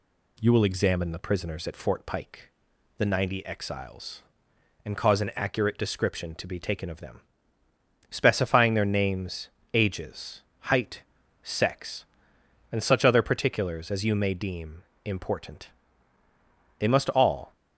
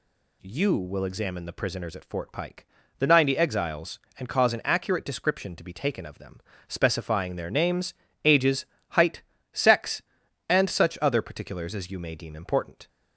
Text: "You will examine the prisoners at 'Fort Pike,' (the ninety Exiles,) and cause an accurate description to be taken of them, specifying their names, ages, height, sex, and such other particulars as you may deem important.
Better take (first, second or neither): second